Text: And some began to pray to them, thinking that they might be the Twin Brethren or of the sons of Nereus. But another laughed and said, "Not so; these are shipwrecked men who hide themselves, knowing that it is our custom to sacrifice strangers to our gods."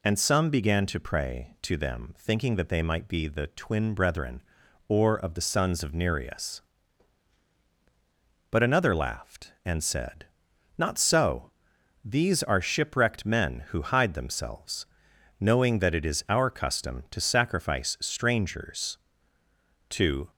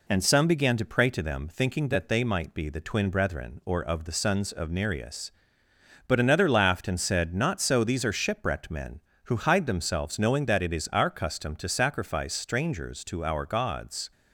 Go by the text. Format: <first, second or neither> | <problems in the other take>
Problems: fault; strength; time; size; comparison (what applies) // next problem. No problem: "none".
second | stops before "our gods"; at 20.2 s